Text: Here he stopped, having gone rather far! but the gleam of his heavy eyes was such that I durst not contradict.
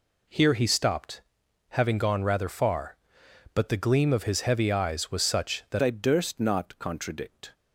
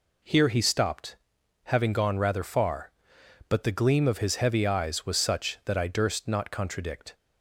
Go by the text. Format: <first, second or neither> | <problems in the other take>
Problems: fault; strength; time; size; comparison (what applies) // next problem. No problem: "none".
second | changes voice at "I"; from 5.8 s on; 1.7 s long